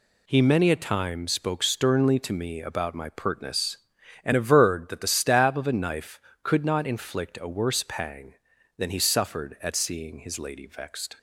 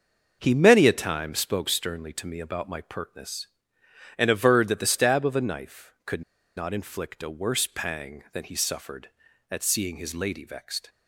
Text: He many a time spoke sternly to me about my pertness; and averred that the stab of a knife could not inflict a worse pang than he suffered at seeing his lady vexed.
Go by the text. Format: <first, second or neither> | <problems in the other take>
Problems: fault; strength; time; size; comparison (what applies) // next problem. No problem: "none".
first | starts louder than the rest; until 1.4 s; 6.5 dB // pauses between "could" and "not"; slight; at 6.2 s; 0.34 s long